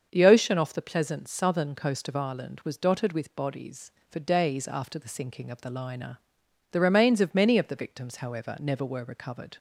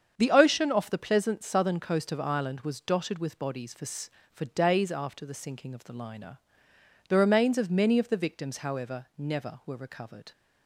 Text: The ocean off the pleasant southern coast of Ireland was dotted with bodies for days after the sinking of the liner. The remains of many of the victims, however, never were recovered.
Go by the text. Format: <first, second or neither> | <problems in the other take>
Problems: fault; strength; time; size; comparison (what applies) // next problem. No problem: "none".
first | starts louder than the rest; strong; until 1.1 s; 7.5 dB; also in the first // says "for" twice; at 4.3 s